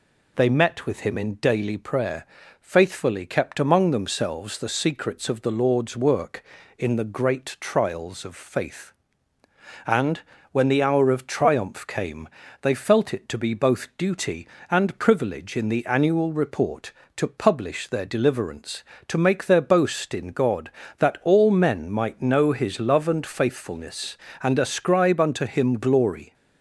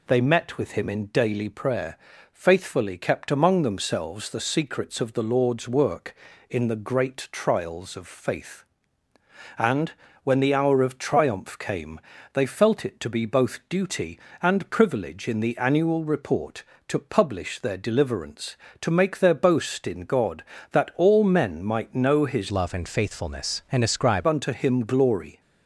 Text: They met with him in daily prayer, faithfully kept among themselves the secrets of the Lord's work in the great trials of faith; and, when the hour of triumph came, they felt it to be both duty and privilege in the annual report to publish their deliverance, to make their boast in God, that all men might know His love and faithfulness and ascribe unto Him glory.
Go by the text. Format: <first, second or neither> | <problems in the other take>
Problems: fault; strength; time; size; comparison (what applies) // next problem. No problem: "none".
first | changes voice from "love" to "ascribe"; from 22.5 to 24.2 s; 1.7 s long